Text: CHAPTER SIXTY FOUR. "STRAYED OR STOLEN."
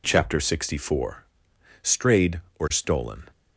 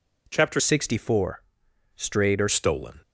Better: first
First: none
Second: changes voice from "SIXTY" to "OR"; from 0.5 to 2.4 s; 1.9 s long

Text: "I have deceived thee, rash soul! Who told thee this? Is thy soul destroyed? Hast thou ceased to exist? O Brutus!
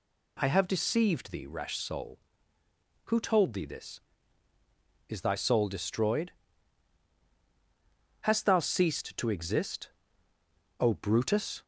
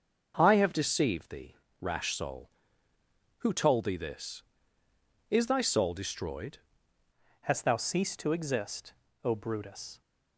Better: first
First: none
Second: starts louder than the rest; until 1.3 s; 6.5 dB // changes voice at "Hast"; from 7.4 s on; 2.6 s long

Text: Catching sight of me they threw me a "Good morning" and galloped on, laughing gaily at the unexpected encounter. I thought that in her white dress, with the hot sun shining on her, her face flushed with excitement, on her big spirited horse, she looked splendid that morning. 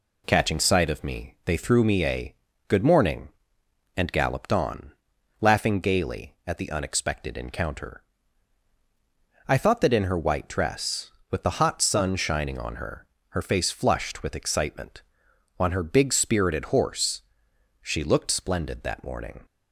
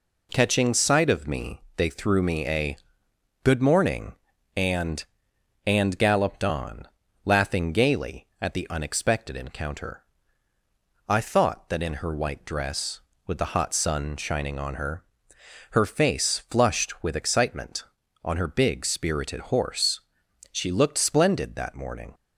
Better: first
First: pauses between "a" and "Good"; slight; at 2.3 s; 0.32 s long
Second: pauses between "me" and "they"; slight; at 1.6 s; 0.16 s long // pauses between "a" and "Good"; noticeable; at 2.7 s; 0.66 s long // says "and" twice; at 5.6 s

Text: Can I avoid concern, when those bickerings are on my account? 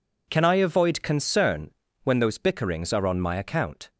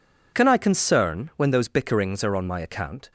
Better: first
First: none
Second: skips "avoid"; at 0.5 s

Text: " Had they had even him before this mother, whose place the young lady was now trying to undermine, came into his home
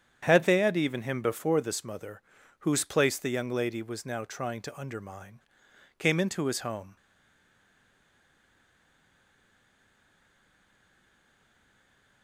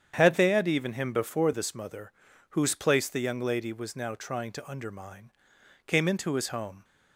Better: second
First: starts louder than the rest; strong; until 1.2 s; 8.5 dB // stays silent after the last word; strong; from 6.9 s on; 5.3 s long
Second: starts louder than the rest; strong; until 1.1 s; 8.5 dB

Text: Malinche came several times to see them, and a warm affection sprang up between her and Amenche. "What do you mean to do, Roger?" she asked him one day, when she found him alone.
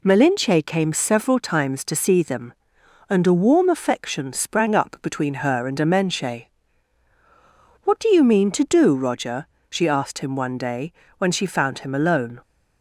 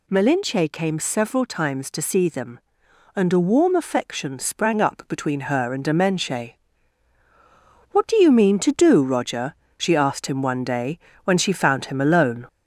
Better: first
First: none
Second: gets louder; slight; throughout; 3 dB

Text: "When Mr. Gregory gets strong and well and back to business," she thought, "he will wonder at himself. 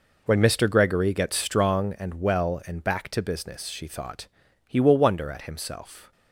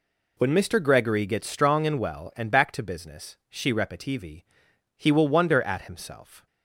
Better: first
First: none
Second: says "repetivi" for "thought"; at 3.7 s

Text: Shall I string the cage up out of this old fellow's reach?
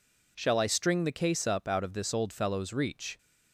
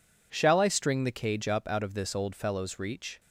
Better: second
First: says "case" for "cage"; at 1.1 s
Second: none

